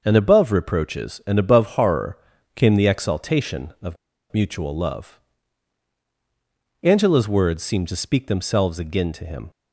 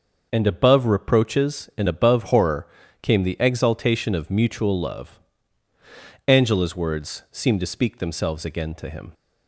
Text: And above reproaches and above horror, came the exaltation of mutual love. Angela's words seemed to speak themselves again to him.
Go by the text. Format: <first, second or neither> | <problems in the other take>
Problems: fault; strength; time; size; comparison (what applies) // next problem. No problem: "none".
second | starts louder than the rest; noticeable; until 1.0 s; 6 dB; noticeable in the second // pauses between "of" and "mutual"; at 3.9 s; 0.37 s long